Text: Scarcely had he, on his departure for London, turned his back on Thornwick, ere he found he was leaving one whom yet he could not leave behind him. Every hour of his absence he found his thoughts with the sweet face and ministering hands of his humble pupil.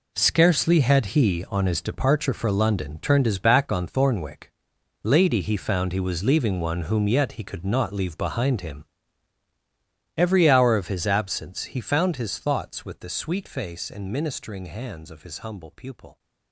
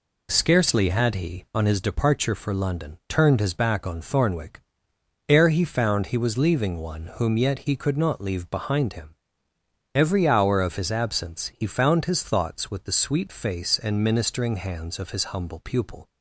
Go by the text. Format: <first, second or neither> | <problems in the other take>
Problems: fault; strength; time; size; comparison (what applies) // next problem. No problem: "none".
second | says "lady" for "ere"; at 5.0 s